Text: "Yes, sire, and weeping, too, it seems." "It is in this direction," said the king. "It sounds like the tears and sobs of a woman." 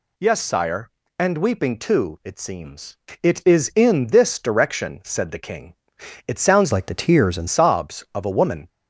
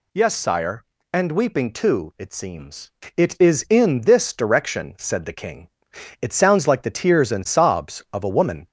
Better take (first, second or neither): second